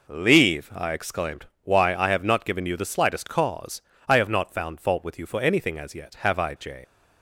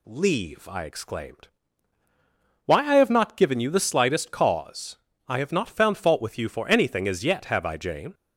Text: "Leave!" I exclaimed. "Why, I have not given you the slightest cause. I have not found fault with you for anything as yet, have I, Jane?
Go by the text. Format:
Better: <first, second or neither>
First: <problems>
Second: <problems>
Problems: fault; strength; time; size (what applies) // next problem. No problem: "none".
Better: second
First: leaves "Jane" unfinished; at 6.8 s; 135 ms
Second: none